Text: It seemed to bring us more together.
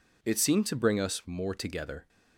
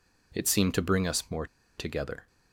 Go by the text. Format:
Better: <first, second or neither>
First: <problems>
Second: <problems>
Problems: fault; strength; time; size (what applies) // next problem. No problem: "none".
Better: first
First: none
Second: pauses between "more" and "together"; slight; at 1.4 s; 0.32 s long